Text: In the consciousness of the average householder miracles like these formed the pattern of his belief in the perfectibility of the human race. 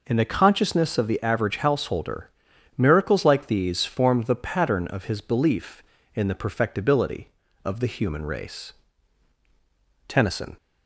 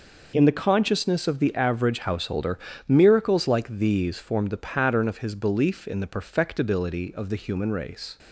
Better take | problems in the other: second | pauses between "householder" and "miracles"; noticeable; at 2.3 s; 0.46 s long; slight in the second // goes on to say "Tennyson"; slight; from 10.0 s on; 0.48 s long

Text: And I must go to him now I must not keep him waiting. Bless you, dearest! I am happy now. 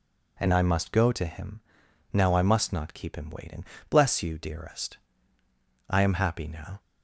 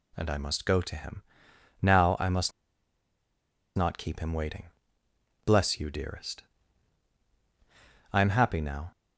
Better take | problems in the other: first | pauses between "him" and "now"; noticeable; at 1.2 s; 0.60 s long; noticeable in the first // pauses between "must" and "not"; strong; at 2.5 s; 1.2 s long

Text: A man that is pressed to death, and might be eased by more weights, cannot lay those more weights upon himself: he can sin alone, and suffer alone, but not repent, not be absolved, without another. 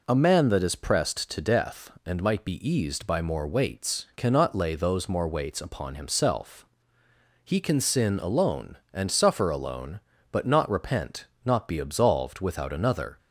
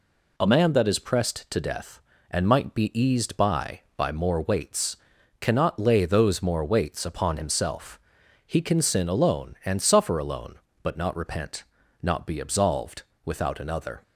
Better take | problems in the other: first | says "by" twice; at 3.9 s

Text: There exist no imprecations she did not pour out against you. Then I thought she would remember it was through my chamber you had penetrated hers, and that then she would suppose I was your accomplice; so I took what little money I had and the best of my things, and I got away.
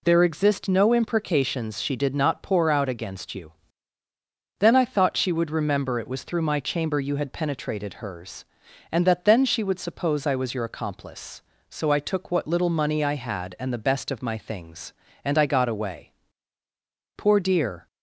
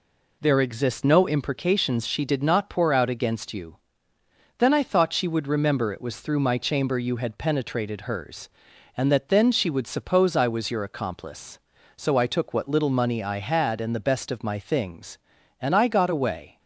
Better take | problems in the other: second | goes on to say "Poor dear"; noticeable; from 17.1 s on; 0.70 s long

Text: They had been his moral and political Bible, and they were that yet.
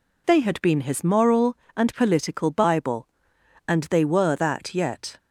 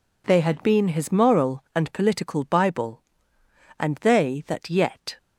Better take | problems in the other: first | skips "were"; at 4.4 s

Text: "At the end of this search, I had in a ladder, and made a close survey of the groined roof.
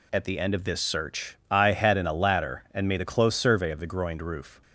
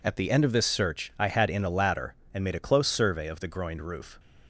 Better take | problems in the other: neither | none

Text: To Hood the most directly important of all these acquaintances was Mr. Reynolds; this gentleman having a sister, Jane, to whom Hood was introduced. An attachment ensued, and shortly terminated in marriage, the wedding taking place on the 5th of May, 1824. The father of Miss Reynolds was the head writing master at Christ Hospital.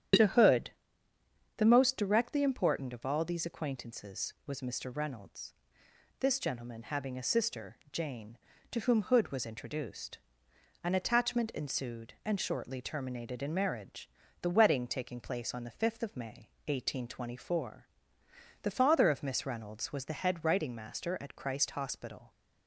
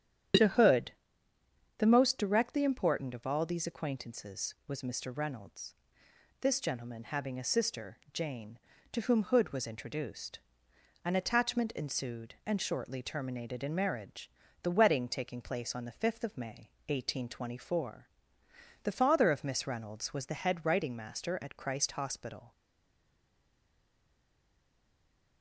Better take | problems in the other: first | starts louder than the rest; strong; until 2.2 s; 9.5 dB; strong in the first // pauses between "Hood" and "the"; noticeable; at 0.9 s; 0.86 s long; noticeable in the first // stays silent after the last word; strong; from 22.5 s on; 2.9 s long

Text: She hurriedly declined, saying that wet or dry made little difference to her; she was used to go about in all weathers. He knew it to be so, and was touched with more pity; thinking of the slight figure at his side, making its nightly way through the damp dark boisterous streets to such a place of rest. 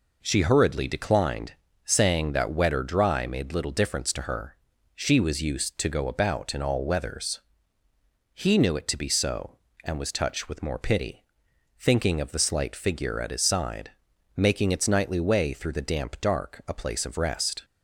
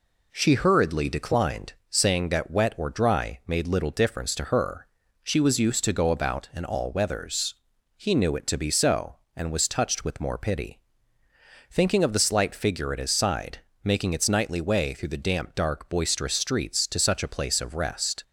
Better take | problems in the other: second | skips "boisterous streets to such"; at 16.6 s

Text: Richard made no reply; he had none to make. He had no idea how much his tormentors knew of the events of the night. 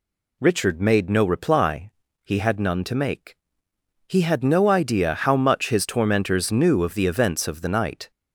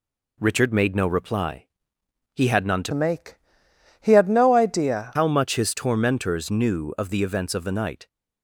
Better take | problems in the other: first | changes voice from "make" to "idea"; from 2.9 to 5.1 s; 2.2 s long

